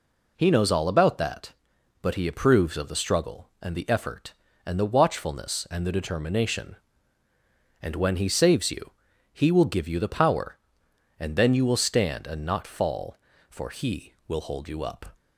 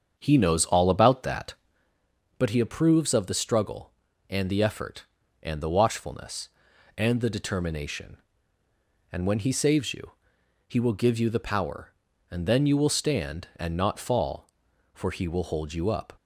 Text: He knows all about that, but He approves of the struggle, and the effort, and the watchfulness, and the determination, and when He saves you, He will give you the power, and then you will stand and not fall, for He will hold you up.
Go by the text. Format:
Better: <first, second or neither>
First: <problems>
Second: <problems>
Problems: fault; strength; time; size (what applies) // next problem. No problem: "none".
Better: first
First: none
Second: starts louder than the rest; strong; until 1.9 s; 7.5 dB